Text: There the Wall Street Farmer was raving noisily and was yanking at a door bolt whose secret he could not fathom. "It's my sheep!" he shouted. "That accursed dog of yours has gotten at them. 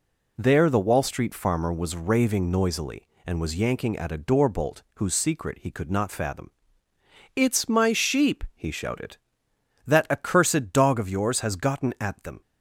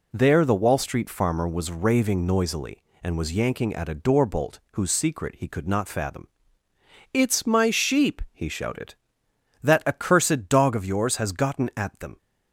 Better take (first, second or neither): neither